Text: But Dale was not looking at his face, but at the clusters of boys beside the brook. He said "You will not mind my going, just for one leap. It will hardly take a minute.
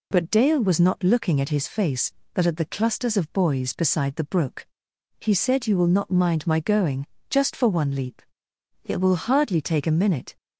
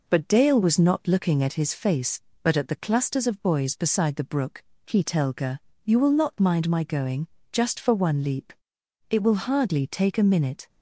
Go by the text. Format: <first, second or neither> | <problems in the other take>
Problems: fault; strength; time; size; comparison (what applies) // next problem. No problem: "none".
first | says "telga" for "said"; at 5.0 s